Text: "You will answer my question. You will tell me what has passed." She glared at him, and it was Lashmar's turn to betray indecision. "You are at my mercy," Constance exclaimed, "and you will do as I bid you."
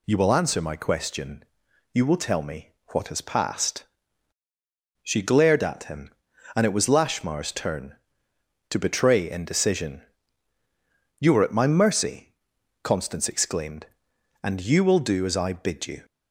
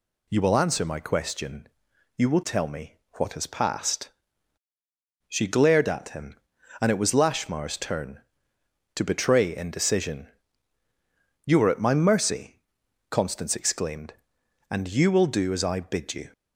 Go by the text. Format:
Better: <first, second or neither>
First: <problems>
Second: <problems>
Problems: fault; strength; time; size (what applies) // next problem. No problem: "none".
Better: neither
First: pauses between "me" and "what"; slight; at 2.7 s; 0.20 s long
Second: pauses between "me" and "what"; slight; at 2.9 s; 0.20 s long